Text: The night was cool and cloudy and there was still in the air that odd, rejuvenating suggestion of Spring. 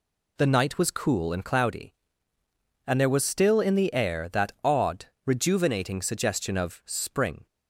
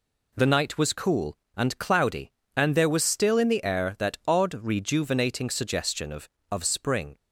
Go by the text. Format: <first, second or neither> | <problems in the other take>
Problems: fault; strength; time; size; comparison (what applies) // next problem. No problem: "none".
first | says "of" twice; at 6.5 s